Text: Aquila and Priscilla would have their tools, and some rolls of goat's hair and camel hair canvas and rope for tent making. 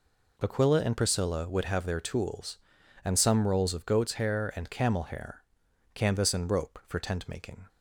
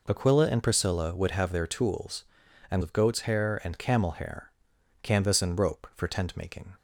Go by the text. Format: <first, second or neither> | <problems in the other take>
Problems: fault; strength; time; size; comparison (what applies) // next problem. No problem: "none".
first | skips "some rolls"; at 2.8 s // pauses between "hair" and "canvas"; noticeable; at 4.5 s; 0.52 s long; noticeable in the first